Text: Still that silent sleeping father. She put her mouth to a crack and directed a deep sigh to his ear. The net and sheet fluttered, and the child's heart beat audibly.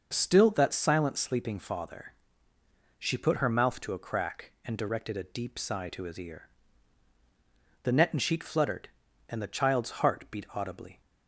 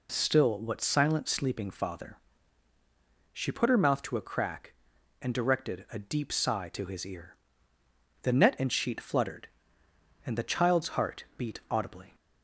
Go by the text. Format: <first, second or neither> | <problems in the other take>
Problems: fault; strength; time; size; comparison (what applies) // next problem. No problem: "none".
first | says "what" for "that"; at 0.5 s